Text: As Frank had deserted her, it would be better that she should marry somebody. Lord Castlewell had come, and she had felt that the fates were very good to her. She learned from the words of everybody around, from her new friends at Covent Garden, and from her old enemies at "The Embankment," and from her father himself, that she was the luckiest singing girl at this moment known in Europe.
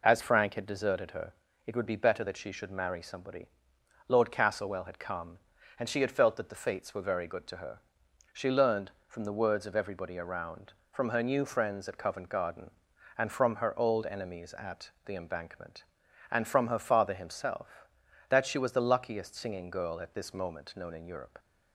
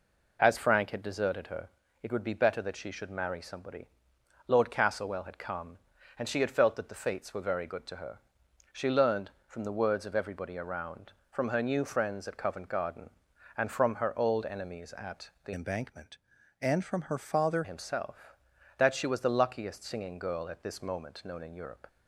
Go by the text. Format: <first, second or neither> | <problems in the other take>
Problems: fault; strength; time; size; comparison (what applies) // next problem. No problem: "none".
first | pauses between "at" and "The"; slight; at 15.2 s; 0.16 s long; slight in the first // changes voice from "Embankment" to "father"; from 15.5 to 17.6 s; 2.1 s long